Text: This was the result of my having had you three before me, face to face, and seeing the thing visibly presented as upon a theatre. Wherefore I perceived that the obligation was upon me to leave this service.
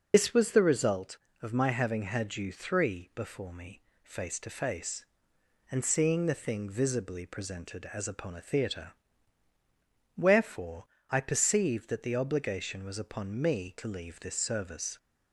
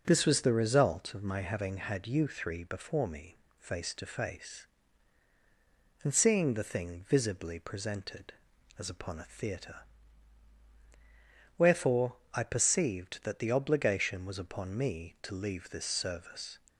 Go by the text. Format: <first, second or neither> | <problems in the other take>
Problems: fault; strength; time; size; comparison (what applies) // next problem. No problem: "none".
second | loses the start of "This"; at 0.1 s; 90 ms // pauses between "Wherefore" and "I"; slight; at 10.8 s; 0.24 s long; slight in the second